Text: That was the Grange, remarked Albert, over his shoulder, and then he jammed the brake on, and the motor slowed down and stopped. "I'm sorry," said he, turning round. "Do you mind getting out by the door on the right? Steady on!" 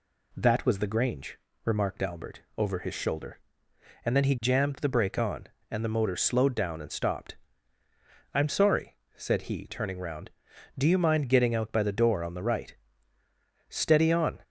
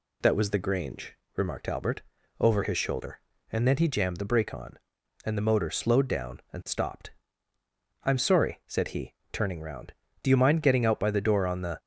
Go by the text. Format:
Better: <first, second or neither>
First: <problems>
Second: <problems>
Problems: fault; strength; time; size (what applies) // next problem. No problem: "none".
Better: first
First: none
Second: stops before "right Steady on"; at 11.7 s